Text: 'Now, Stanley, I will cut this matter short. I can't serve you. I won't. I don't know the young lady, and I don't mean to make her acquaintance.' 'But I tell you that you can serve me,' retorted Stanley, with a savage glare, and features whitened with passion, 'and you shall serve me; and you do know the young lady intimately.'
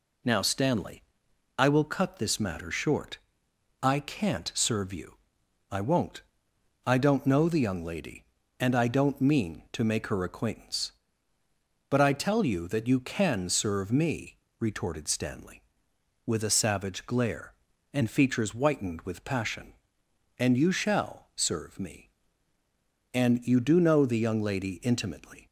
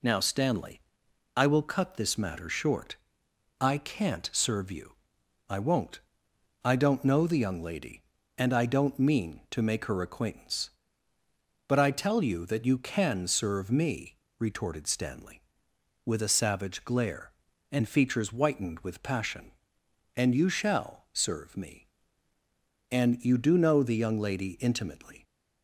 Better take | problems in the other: neither | none

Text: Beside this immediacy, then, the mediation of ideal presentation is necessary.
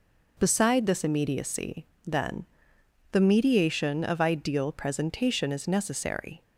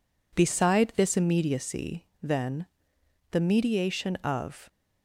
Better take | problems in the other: first | stops before "ideal presentation is necessary"; at 4.6 s

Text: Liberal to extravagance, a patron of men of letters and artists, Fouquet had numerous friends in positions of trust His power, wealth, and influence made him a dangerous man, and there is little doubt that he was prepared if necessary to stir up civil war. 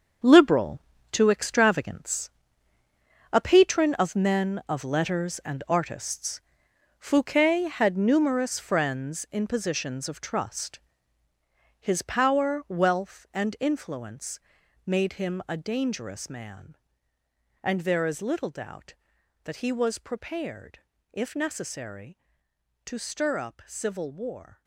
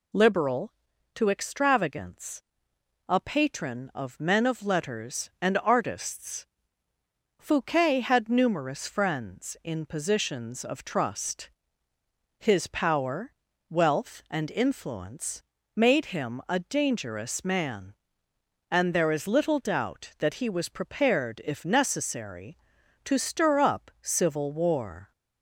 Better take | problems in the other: second | gets quieter; strong; throughout; 12 dB // pauses between "trust" and "His"; at 10.7 s; 1.0 s long; noticeable in the second // pauses between "influence" and "made"; noticeable; at 14.3 s; 0.48 s long; slight in the second // pauses between "prepared" and "if"; slight; at 20.7 s; 0.32 s long

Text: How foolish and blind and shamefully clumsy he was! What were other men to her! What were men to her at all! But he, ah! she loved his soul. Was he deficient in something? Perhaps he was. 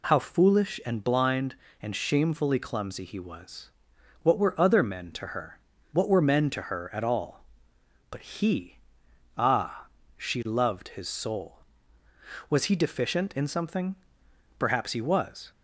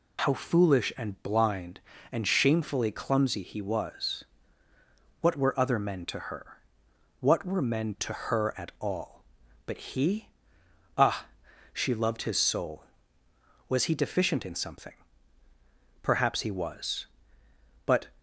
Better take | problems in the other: first | goes on to say "But"; slight; from 17.8 s on; 0.28 s long

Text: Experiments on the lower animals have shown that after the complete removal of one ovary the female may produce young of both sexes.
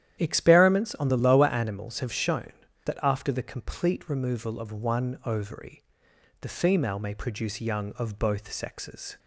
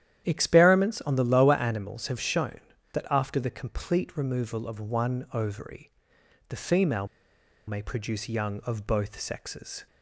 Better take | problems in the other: first | starts louder than the rest; strong; until 1.2 s; 11 dB; strong in the first // pauses between "ovary" and "the"; noticeable; at 5.9 s; 0.58 s long; noticeable in the first // pauses between "female" and "may"; noticeable; at 7.0 s; 0.61 s long

